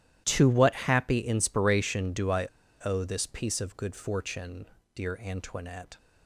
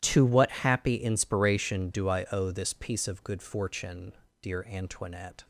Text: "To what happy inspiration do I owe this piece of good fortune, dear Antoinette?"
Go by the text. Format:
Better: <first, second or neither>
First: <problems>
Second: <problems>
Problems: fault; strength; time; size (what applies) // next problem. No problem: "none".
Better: second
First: starts louder than the rest; strong; until 1.2 s; 13 dB // pauses between "I" and "owe"; at 2.4 s; 0.37 s long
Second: starts louder than the rest; strong; until 1.0 s; 13 dB